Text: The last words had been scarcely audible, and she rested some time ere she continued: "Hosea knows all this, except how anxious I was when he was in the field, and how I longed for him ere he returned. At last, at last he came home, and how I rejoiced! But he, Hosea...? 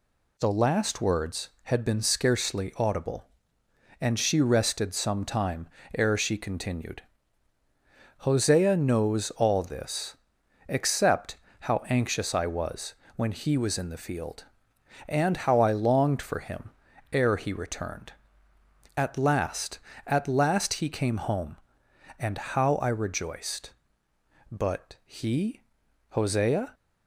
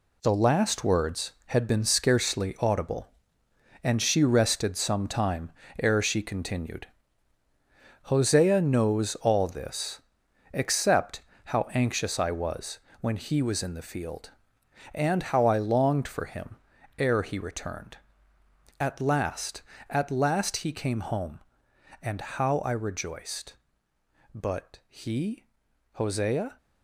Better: first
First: pauses between "time" and "ere"; slight; at 5.6 s; 0.30 s long // pauses between "except" and "how"; slight; at 11.3 s; 0.24 s long // pauses between "was" and "when"; slight; at 12.9 s; 0.20 s long // pauses between "him" and "ere"; at 16.7 s; 0.40 s long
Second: gets quieter; strong; throughout; 8.5 dB // pauses between "time" and "ere"; slight; at 5.4 s; 0.32 s long // pauses between "except" and "how"; slight; at 11.2 s; 0.24 s long // pauses between "was" and "when"; slight; at 12.7 s; 0.20 s long // pauses between "him" and "ere"; at 16.5 s; 0.40 s long

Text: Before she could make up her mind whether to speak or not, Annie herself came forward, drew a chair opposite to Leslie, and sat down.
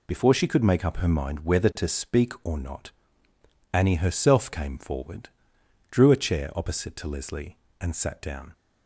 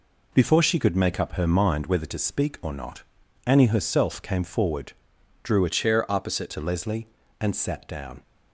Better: first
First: none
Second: changes voice from "chair" to "opposite"; from 5.7 to 6.5 s; 0.8 s long

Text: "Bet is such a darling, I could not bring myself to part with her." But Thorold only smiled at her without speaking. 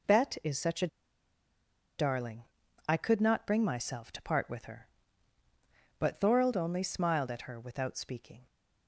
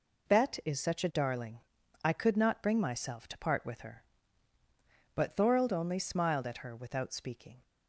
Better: second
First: pauses between "a" and "darling"; at 0.8 s; 1.0 s long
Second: none

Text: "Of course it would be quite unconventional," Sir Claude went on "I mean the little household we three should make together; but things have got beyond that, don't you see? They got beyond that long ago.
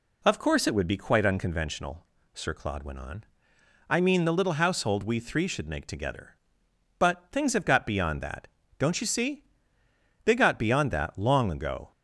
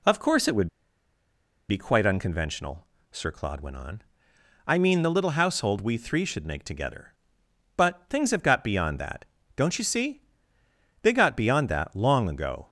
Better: first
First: pauses between "on" and "I"; noticeable; at 3.2 s; 0.66 s long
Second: pauses between "would" and "be"; at 0.6 s; 1.0 s long // pauses between "on" and "I"; noticeable; at 4.0 s; 0.66 s long

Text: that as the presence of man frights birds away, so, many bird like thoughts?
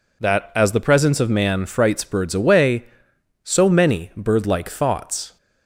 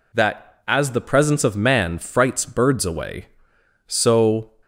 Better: first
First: none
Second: stops before "many bird like thoughts"; at 4.6 s

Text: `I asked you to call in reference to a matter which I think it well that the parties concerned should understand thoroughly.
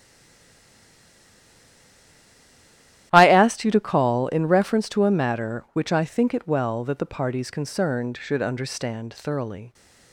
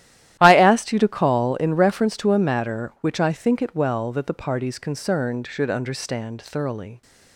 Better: second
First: stays silent before the first word; strong; until 3.1 s; 3.1 s long // starts louder than the rest; strong; until 4.1 s; 13 dB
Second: starts louder than the rest; strong; until 1.4 s; 13 dB

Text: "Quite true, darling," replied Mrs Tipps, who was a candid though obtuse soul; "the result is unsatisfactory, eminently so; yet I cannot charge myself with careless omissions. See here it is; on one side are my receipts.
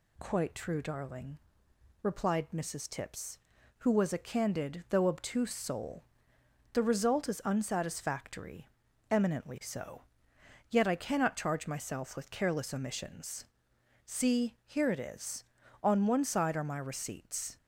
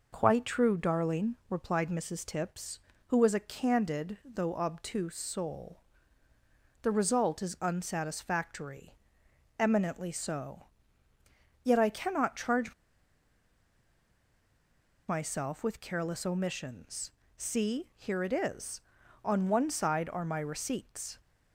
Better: first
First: none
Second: pauses between "charge" and "myself"; strong; at 12.7 s; 2.3 s long

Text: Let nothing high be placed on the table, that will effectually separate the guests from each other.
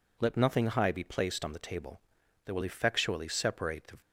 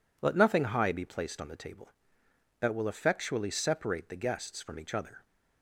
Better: second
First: stops before "guests from each other"; at 4.0 s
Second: none

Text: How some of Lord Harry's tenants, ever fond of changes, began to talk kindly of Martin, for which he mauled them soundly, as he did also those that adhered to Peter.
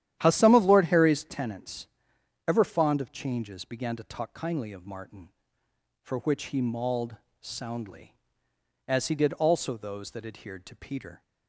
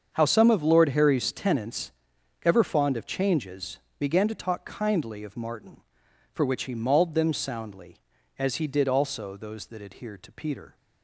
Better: second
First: starts louder than the rest; strong; until 1.2 s; 11.5 dB // skips "them"; at 7.2 s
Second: starts louder than the rest; until 1.1 s; 7 dB

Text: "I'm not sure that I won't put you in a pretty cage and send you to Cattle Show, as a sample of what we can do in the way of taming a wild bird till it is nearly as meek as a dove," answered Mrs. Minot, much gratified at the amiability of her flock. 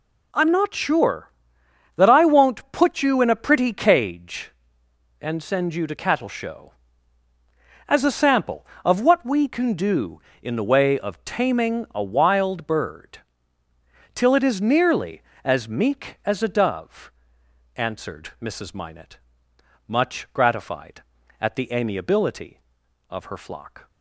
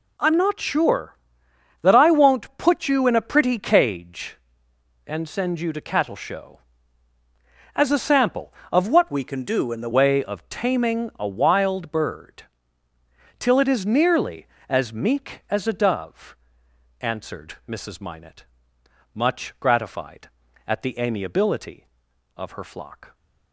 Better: first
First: pauses between "bird" and "till"; noticeable; at 13.1 s; 0.94 s long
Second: changes voice from "we" to "the"; from 9.1 to 9.9 s; 0.8 s long // pauses between "bird" and "till"; noticeable; at 12.4 s; 0.94 s long

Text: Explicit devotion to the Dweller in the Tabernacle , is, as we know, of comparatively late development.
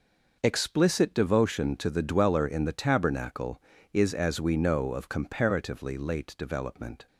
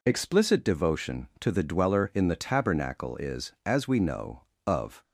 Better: first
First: none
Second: stops before "comparatively late development"; at 5.0 s

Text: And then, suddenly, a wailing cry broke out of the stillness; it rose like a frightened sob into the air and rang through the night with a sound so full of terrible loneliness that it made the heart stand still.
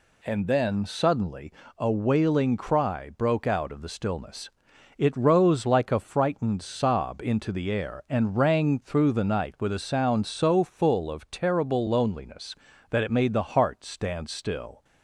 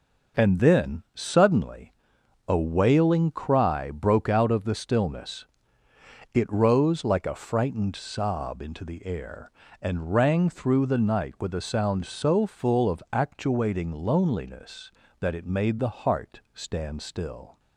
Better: first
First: none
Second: says "actuating" for "terrible"; at 13.1 s

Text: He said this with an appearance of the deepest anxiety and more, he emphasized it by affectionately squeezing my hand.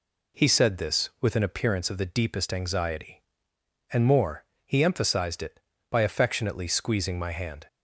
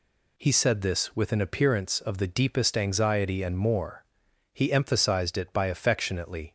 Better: first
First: none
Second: stops before "squeezing my hand"; at 6.4 s

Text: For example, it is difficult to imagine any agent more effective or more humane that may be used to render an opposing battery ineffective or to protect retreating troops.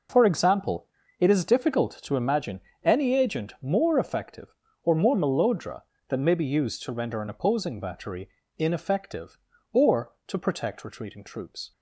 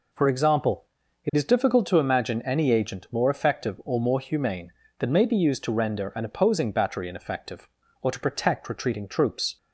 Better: second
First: pauses between "imagine" and "any"; slight; at 2.5 s; 0.24 s long // says "melodra" for "humane"; at 5.1 s // pauses between "battery" and "ineffective"; slight; at 8.2 s; 0.28 s long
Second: none

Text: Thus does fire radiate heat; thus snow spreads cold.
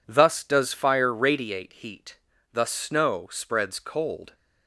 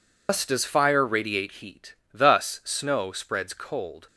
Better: first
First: none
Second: loses the start of "Thus"; at 0.2 s; 125 ms

